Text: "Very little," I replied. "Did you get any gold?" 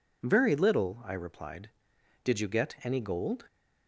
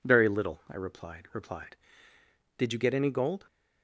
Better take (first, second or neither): first